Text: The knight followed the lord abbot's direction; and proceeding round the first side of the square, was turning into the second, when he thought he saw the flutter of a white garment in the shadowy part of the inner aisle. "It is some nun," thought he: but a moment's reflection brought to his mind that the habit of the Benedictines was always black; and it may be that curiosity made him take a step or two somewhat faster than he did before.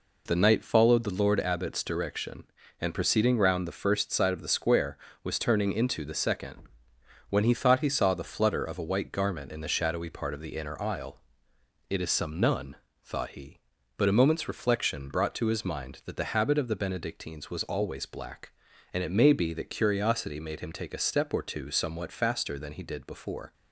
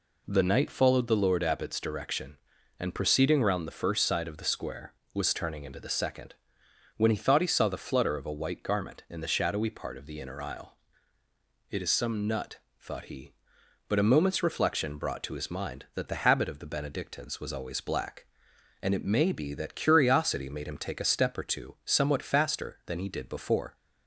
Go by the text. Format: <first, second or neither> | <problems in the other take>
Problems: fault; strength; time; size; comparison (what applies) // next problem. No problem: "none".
first | says "nut" for "nun"; at 12.2 s